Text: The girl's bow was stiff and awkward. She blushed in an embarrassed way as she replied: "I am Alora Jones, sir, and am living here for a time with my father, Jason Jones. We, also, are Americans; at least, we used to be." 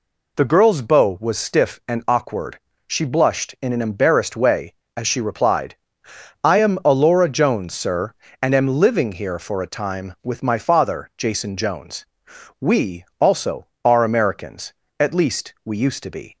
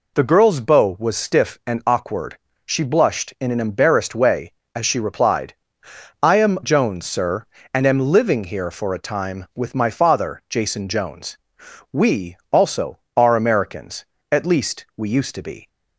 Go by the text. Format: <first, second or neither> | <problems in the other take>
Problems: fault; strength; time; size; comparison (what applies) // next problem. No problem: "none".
first | skips "Alora"; at 6.6 s